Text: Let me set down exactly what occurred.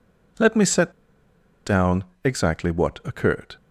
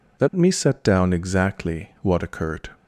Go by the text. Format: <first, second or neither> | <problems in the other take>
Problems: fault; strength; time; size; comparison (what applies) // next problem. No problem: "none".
second | pauses between "set" and "down"; noticeable; at 0.9 s; 0.75 s long // pauses between "down" and "exactly"; slight; at 2.0 s; 0.20 s long